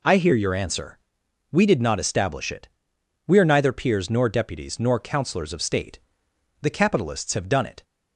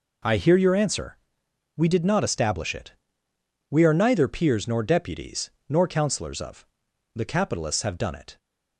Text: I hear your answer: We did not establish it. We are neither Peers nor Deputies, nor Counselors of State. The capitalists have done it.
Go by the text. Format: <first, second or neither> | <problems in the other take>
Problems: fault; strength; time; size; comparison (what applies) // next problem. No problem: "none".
first | skips "State"; at 6.8 s